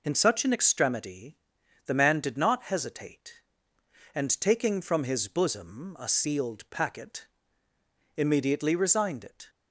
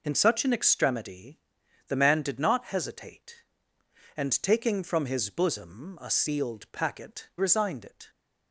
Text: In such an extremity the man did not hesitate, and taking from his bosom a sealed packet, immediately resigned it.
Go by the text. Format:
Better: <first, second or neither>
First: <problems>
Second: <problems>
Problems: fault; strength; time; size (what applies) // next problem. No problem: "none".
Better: first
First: pauses between "extremity" and "the"; noticeable; at 1.3 s; 0.48 s long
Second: pauses between "extremity" and "the"; noticeable; at 1.3 s; 0.48 s long // skips "immediately"; at 7.3 s